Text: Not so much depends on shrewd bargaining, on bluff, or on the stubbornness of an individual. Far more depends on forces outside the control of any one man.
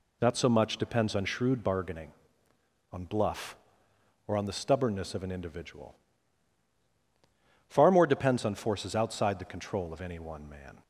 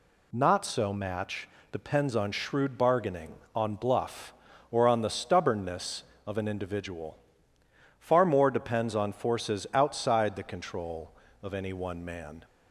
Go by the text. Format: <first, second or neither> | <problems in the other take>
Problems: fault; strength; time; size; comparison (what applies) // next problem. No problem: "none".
first | says "match" for "much"; at 0.9 s